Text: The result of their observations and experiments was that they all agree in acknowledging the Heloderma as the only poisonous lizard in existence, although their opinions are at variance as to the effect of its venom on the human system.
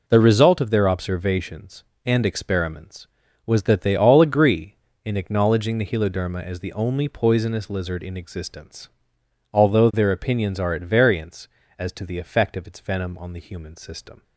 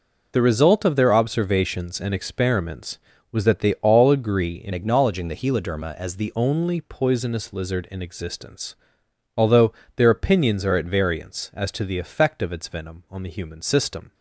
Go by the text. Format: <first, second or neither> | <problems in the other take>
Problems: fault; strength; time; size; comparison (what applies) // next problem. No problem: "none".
first | changes voice from "acknowledging" to "the"; from 4.7 to 6.3 s; 1.6 s long // pauses between "although" and "their"; slight; at 9.7 s; 0.24 s long